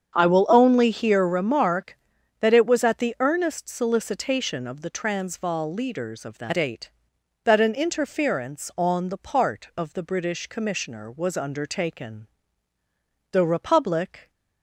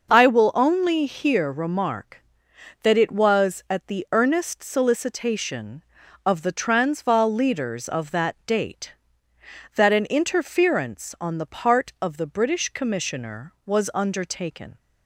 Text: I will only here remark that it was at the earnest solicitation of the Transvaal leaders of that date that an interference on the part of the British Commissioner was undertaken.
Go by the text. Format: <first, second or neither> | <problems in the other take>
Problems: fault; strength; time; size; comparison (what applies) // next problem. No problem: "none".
second | starts louder than the rest; strong; until 1.2 s; 8 dB // goes on to say "The Republic"; noticeable; from 13.3 s on; 0.98 s long